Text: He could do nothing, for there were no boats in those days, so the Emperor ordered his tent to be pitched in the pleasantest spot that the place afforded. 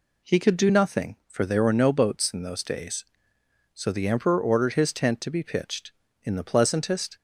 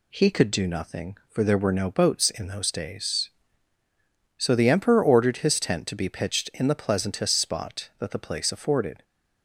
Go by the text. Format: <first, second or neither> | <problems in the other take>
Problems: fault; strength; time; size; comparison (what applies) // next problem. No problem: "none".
second | stops before "spot that the place afforded"; at 7.1 s